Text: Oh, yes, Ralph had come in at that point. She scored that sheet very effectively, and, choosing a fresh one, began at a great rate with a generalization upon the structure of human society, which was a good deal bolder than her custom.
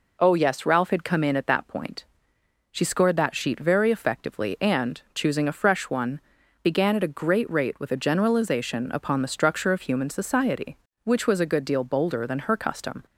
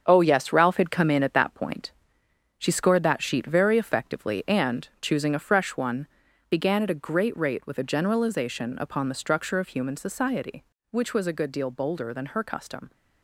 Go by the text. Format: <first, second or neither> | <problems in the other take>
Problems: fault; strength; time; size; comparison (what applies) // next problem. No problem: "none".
first | gets quieter; strong; throughout; 8 dB